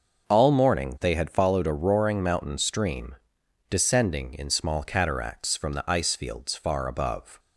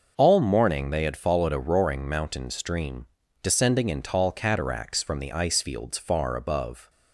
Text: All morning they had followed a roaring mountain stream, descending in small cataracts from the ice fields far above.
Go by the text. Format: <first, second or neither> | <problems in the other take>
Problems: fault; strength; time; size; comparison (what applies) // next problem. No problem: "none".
first | starts louder than the rest; noticeable; until 1.1 s; 6 dB // says "tall" for "small"; at 4.0 s